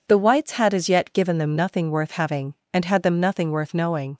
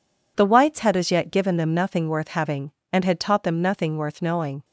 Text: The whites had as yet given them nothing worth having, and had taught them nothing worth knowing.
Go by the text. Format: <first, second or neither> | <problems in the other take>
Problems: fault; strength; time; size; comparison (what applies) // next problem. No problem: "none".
second | skips "taught"; at 3.0 s